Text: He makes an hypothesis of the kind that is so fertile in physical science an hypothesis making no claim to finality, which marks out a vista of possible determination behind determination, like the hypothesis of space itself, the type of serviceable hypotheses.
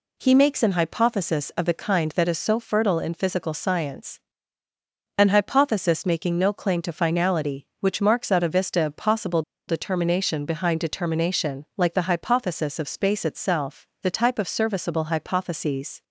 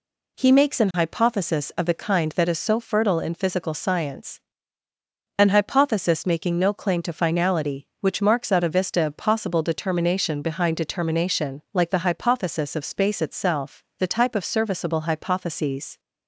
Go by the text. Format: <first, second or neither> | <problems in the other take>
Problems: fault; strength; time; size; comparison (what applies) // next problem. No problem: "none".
second | pauses between "science" and "an"; at 4.1 s; 1.0 s long; also in the second // pauses between "possible" and "determination"; slight; at 9.4 s; 0.26 s long